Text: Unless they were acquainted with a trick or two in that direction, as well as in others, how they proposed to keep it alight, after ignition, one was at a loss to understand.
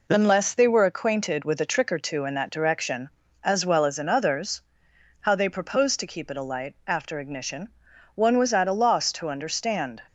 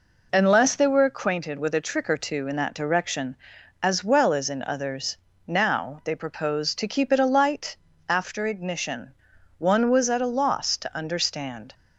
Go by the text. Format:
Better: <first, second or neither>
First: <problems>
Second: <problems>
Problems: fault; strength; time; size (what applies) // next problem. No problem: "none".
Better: first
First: none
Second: says "now" for "how"; at 5.4 s